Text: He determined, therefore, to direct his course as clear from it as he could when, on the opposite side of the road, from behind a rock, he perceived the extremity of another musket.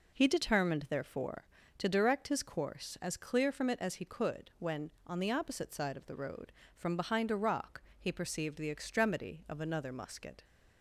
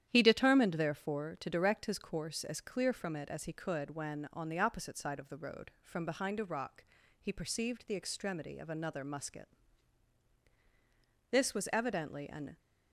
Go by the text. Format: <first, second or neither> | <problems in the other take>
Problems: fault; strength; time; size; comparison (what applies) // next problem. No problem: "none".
first | starts louder than the rest; strong; until 1.1 s; 10.5 dB // goes on to say "This was evidently an"; noticeable; from 11.2 s on; 1.2 s long